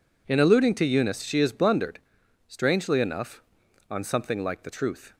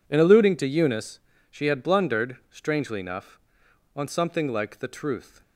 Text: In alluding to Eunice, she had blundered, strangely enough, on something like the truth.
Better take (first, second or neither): second